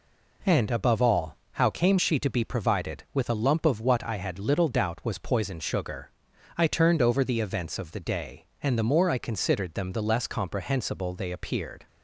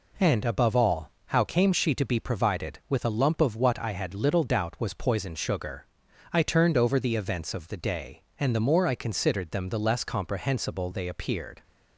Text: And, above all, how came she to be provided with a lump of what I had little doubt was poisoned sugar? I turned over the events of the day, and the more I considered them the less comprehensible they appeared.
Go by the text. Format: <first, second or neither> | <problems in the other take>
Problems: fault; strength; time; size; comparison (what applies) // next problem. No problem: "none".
neither | none